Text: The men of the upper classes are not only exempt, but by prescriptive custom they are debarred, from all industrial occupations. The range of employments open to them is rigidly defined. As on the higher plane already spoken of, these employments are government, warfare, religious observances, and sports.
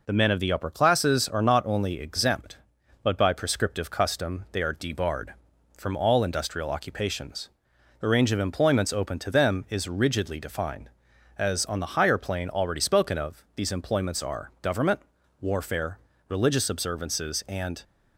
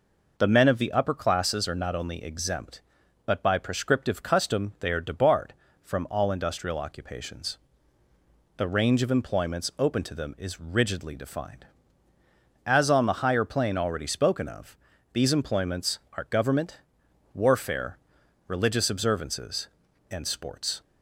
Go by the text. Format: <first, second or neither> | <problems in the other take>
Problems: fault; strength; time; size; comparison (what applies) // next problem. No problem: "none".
second | stops before "sports"; at 17.8 s